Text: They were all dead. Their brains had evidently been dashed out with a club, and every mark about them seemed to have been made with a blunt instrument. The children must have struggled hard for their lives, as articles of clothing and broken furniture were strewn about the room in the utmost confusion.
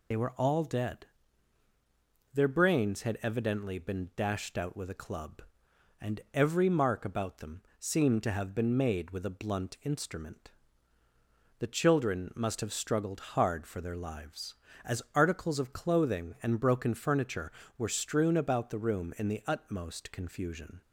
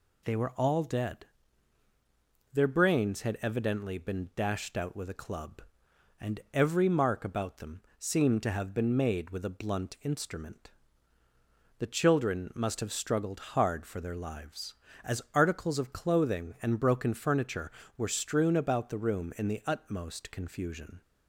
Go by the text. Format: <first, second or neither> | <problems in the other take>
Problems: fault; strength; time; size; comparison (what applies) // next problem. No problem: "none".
second | loses the start of "They"; at 0.1 s; 50 ms // pauses between "them" and "seemed"; slight; at 7.6 s; 0.18 s long; slight in the second